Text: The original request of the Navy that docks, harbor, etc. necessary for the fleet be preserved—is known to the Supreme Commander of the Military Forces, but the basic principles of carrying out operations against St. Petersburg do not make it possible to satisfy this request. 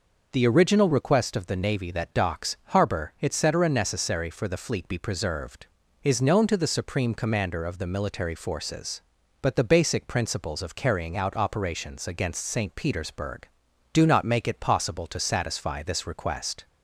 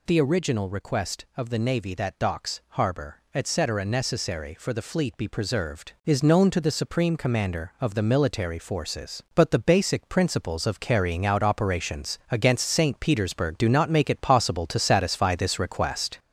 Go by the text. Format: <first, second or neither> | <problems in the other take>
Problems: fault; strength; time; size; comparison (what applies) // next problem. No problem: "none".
first | gets louder; noticeable; throughout; 5 dB